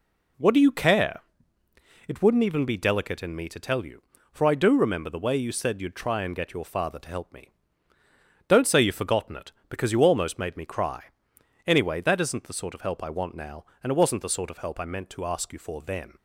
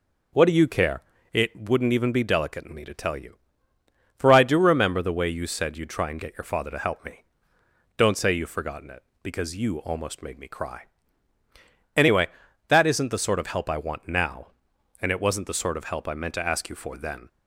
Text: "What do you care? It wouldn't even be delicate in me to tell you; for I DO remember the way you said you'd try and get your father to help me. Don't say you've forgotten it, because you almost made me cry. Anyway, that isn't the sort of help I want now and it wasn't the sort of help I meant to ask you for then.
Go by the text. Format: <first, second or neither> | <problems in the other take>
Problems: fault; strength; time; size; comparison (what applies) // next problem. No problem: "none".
neither | none